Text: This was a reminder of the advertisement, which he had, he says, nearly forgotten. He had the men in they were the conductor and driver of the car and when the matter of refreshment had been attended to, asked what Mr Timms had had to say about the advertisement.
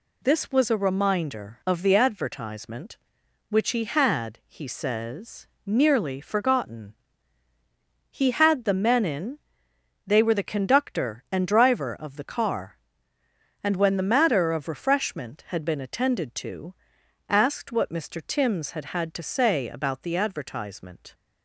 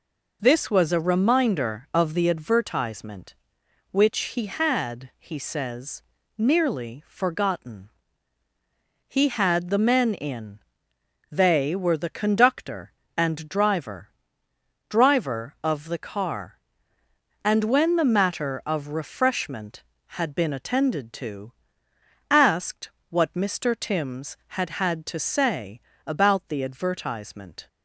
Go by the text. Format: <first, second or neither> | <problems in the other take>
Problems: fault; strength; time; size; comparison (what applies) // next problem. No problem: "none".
first | pauses between "in" and "they"; noticeable; at 10.5 s; 0.72 s long; noticeable in the first // says "driver" twice; at 14.8 s // pauses between "asked" and "what"; slight; at 22.8 s; 0.20 s long // pauses between "say" and "about"; slight; at 25.8 s; 0.24 s long